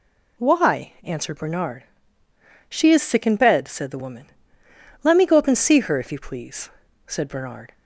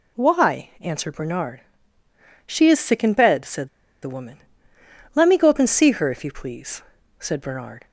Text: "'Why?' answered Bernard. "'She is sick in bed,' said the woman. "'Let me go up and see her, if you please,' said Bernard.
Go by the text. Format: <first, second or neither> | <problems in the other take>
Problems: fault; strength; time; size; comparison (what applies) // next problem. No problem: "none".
first | pauses between "said" and "the"; slight; at 3.6 s; 0.34 s long